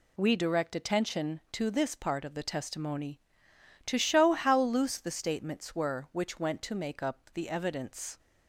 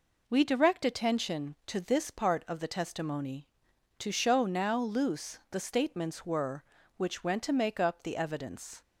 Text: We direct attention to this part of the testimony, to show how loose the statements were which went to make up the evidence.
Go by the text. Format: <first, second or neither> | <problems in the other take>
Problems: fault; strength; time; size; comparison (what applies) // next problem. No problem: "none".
first | says "now" for "how"; at 4.4 s